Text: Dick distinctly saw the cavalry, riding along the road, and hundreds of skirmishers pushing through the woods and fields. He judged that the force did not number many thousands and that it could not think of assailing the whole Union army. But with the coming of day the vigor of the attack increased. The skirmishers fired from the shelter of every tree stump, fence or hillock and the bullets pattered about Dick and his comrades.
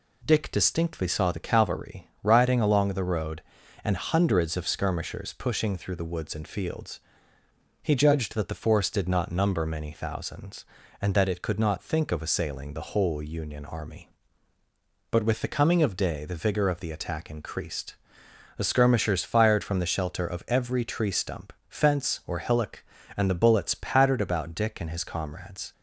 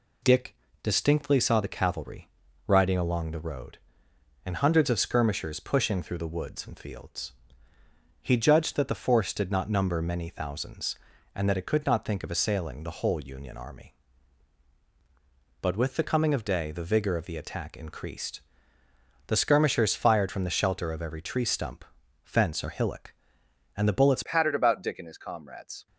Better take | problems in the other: first | pauses between "Dick" and "distinctly"; slight; at 0.5 s; 0.28 s long // changes voice at "pattered"; from 24.2 s on; 1.6 s long

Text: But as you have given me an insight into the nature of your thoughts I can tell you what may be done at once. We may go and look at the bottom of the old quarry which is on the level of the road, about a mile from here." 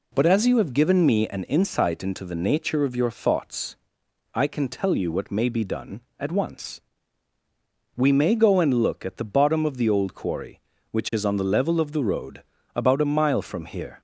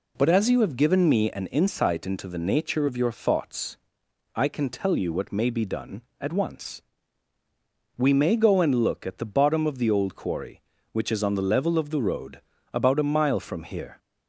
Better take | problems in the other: neither | pauses between "thoughts" and "I"; noticeable; the same in both

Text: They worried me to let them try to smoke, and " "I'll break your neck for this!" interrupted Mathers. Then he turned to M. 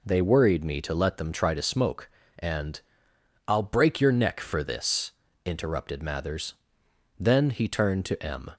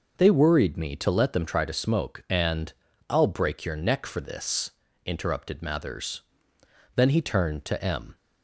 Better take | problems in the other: neither | none

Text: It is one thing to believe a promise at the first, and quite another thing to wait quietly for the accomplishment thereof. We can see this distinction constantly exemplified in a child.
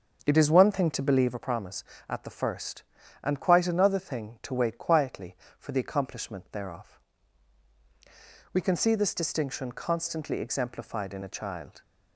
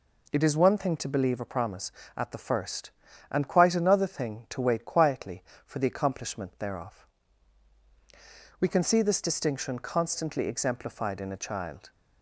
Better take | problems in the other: second | starts louder than the rest; until 1.4 s; 7 dB

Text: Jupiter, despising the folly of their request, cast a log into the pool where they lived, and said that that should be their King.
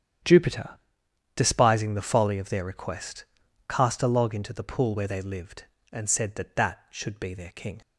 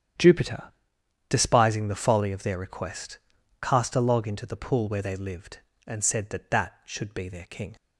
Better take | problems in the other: neither | starts louder than the rest; strong; the same in both

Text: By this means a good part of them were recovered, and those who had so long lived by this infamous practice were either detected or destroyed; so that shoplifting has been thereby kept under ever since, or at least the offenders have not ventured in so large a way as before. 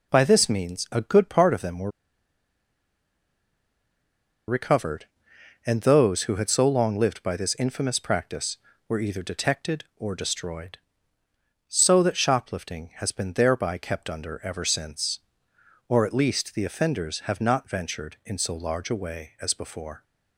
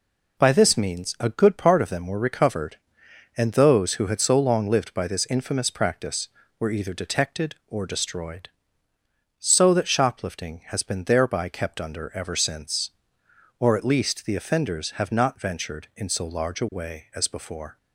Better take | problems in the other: second | pauses between "were" and "recovered"; strong; at 1.8 s; 2.5 s long

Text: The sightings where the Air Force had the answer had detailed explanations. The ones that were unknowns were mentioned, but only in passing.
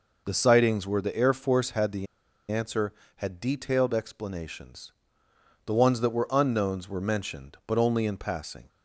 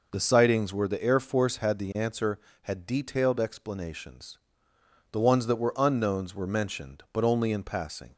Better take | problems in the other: second | pauses between "the" and "answer"; at 2.0 s; 0.43 s long

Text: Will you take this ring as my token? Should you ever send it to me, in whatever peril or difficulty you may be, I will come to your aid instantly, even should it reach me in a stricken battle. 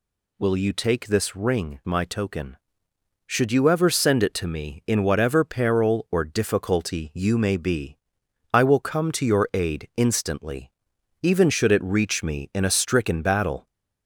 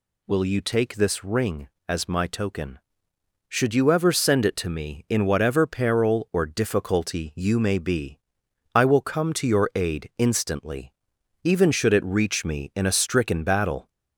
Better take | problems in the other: second | skips "as"; at 1.8 s

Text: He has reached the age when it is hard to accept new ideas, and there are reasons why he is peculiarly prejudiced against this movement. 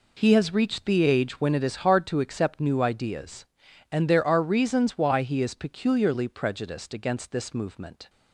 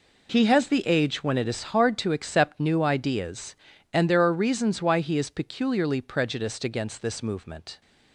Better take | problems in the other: first | skips "reached"; at 0.6 s

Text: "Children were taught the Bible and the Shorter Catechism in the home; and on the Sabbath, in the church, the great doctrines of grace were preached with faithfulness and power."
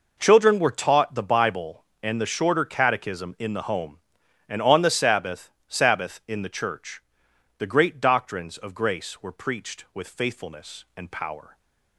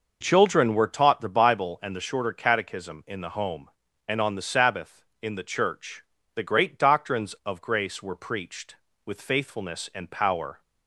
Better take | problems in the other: second | says "Sabbath" twice; at 5.7 s

